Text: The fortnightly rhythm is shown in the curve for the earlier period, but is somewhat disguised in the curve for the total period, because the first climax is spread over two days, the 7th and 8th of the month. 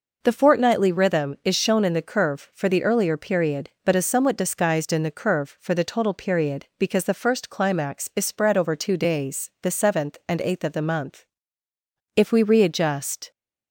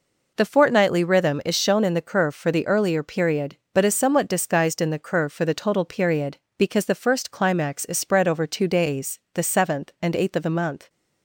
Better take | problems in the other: second | goes on to say "If we readjust"; noticeable; from 12.1 s on; 1.1 s long

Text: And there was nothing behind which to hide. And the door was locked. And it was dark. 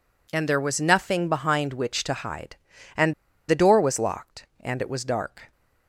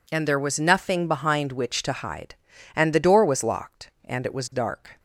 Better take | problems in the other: second | pauses between "And" and "the"; slight; at 3.1 s; 0.35 s long

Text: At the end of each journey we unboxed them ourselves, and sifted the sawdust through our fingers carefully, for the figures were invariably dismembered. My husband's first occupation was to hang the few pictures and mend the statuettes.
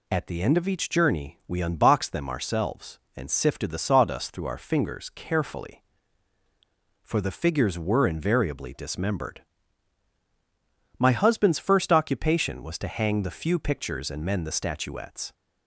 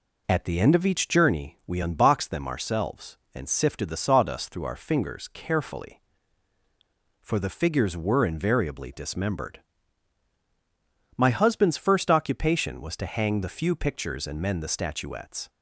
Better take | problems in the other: first | starts louder than the rest; until 1.4 s; 3.5 dB

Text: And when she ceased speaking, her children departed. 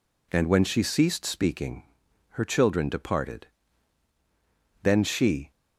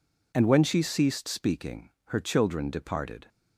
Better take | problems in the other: second | goes on to say "Then she"; noticeable; from 4.8 s on; 0.68 s long

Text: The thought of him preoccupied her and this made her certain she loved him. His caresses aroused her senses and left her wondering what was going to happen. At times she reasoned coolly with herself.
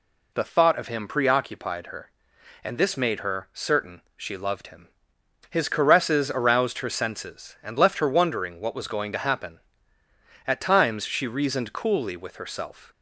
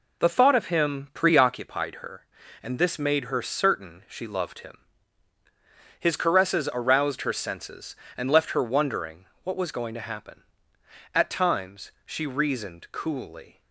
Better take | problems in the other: first | pauses between "wondering" and "what"; slight; at 9.2 s; 0.20 s long // stops before "with herself"; at 13.6 s

